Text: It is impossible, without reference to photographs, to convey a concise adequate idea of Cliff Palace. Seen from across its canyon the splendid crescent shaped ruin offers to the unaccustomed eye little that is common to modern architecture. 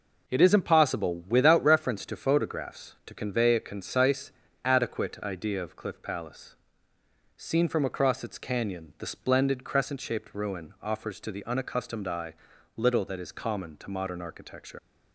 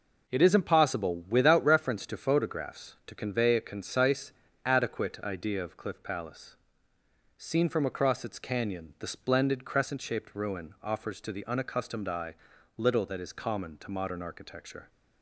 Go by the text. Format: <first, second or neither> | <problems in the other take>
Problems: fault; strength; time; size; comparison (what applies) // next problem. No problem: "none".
second | pauses between "concise" and "adequate"; slight; at 4.3 s; 0.32 s long; slight in the second // pauses between "eye" and "little"; at 12.3 s; 0.44 s long; also in the second // leaves "architecture" unfinished; at 14.7 s; 95 ms